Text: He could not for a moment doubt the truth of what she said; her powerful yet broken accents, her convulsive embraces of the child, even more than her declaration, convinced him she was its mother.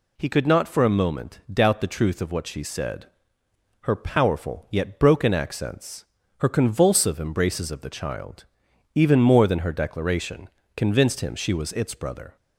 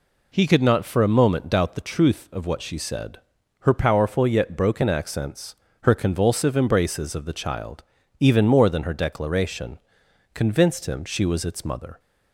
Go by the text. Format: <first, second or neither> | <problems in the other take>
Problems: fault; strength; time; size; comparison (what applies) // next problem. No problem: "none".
second | says "brother" for "mother"; at 11.9 s